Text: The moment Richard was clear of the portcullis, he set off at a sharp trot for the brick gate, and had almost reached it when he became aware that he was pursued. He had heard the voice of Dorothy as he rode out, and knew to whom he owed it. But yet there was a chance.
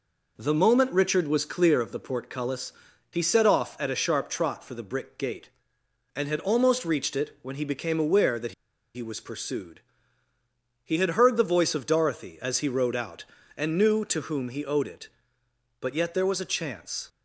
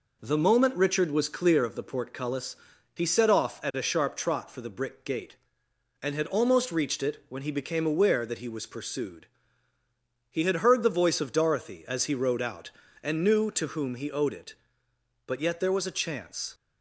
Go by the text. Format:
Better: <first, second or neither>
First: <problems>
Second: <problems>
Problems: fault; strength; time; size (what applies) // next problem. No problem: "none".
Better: second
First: pauses between "that" and "he"; at 8.5 s; 0.43 s long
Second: none